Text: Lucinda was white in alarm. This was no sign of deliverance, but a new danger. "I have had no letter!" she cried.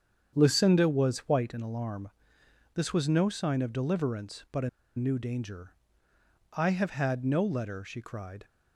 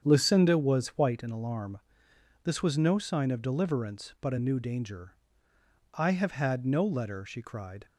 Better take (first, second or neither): second